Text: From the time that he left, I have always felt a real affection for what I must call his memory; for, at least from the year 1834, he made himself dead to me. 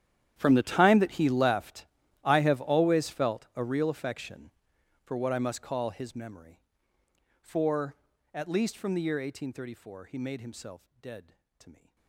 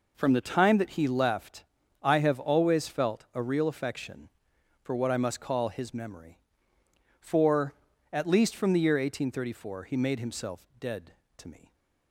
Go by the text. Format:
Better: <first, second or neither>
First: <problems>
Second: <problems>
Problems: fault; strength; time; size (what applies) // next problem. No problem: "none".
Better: second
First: gets quieter; strong; throughout; 20.5 dB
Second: none